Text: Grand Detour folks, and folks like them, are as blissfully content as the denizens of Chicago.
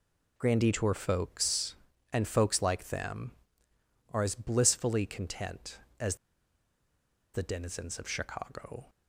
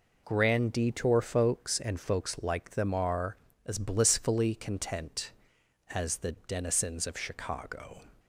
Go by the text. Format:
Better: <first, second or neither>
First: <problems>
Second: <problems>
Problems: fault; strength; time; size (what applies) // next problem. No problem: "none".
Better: second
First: pauses between "as" and "the"; at 6.1 s; 1.1 s long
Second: none